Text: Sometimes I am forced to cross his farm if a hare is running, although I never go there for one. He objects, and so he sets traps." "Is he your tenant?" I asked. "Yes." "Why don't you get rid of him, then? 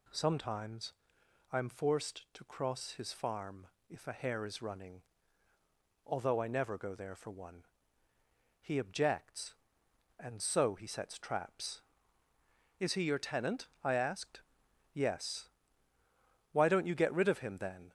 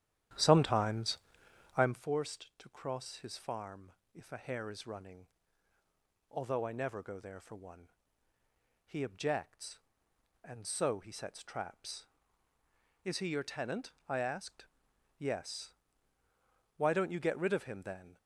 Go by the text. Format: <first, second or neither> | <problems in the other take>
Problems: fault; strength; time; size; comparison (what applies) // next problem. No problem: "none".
first | starts louder than the rest; strong; until 2.0 s; 11 dB // pauses between "Sometimes" and "I"; noticeable; at 1.1 s; 0.58 s long; noticeable in the first // pauses between "farm" and "if"; slight; at 3.9 s; 0.22 s long; slight in the first